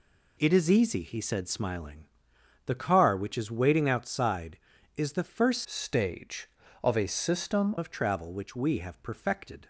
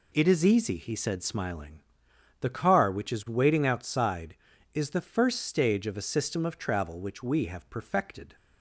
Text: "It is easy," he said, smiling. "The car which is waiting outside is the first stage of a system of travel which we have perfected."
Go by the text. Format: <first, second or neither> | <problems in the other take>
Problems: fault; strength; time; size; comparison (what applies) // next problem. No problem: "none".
second | changes voice from "stage" to "system"; from 5.6 to 7.7 s; 2.1 s long